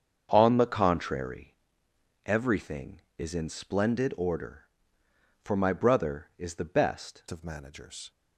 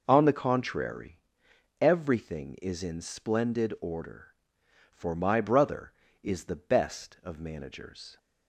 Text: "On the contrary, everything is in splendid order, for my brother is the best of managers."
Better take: second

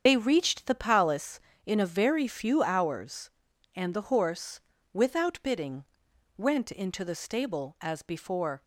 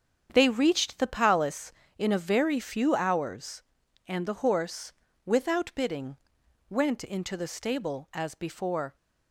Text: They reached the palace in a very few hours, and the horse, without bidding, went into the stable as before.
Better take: second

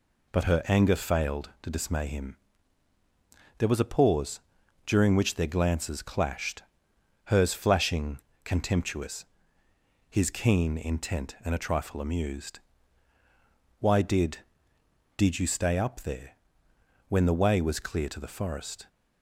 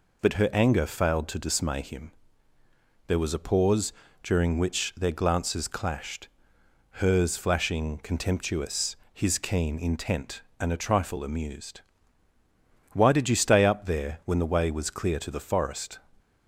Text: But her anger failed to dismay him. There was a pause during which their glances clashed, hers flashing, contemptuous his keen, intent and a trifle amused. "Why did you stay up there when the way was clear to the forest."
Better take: second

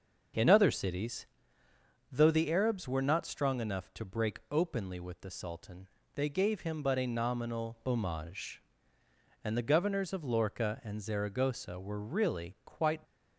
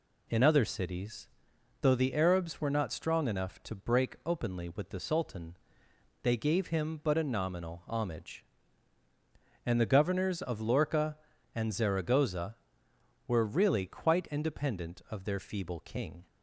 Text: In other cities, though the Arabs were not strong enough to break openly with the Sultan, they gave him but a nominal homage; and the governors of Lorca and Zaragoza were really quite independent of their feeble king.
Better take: second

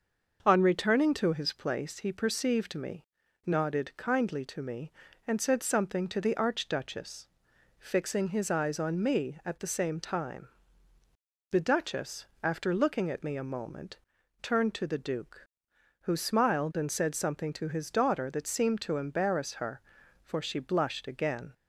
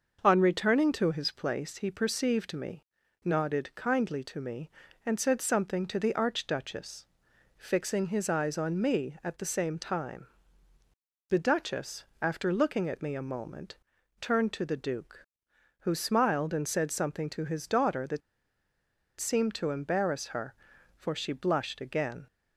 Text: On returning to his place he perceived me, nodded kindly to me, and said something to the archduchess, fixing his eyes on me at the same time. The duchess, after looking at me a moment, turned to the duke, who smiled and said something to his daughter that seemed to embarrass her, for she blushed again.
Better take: first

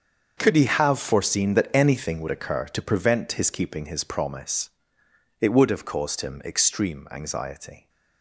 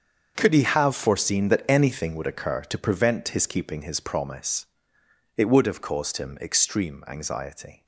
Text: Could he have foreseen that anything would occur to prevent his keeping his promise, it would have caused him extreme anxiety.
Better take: neither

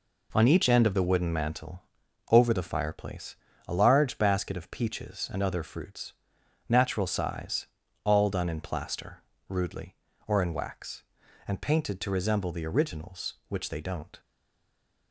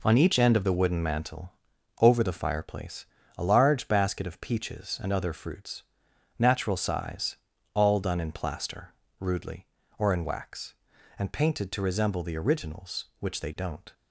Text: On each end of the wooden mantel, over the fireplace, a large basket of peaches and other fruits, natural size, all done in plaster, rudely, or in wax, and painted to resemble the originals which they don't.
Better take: second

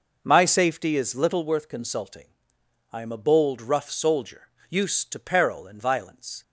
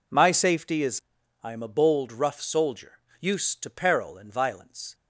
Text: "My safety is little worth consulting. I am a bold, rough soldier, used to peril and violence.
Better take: first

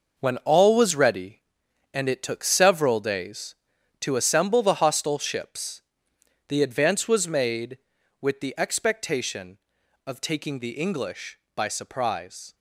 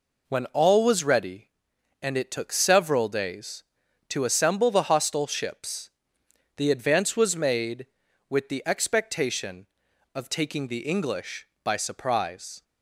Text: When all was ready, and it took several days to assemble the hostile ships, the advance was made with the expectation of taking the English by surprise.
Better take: second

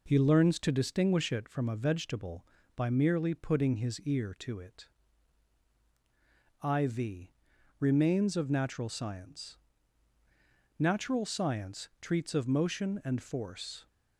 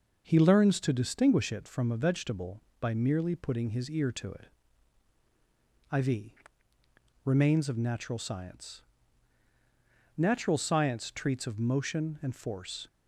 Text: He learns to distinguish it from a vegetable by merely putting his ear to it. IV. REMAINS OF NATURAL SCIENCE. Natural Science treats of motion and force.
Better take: neither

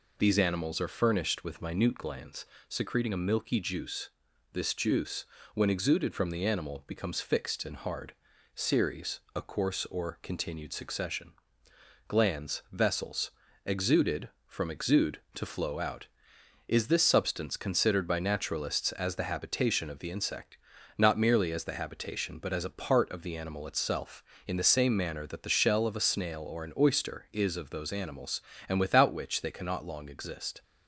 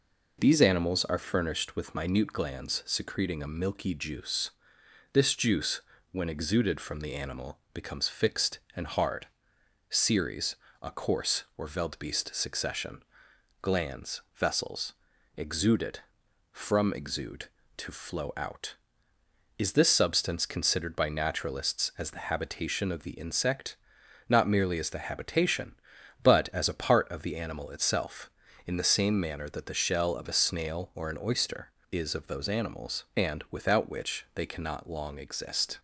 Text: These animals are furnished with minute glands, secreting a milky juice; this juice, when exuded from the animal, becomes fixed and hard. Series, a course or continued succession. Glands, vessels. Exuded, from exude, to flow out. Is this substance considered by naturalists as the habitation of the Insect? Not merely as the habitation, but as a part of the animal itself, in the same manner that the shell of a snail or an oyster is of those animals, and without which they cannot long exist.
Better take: first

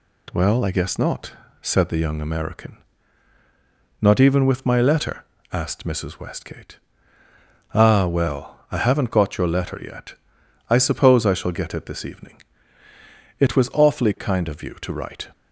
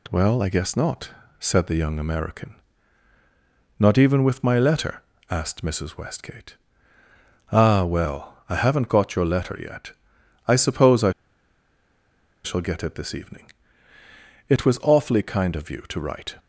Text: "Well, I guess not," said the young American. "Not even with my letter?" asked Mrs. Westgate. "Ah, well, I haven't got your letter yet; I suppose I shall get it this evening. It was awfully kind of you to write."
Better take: first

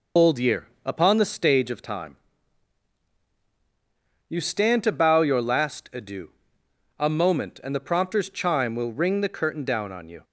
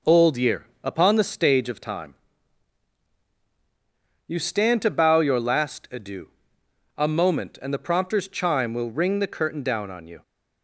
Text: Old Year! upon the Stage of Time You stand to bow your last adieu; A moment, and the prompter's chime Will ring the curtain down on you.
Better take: second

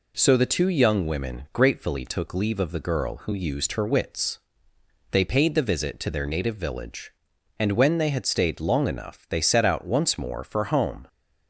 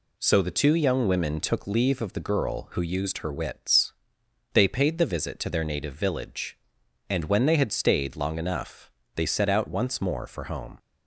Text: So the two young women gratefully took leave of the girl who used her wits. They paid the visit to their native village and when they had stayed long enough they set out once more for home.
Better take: first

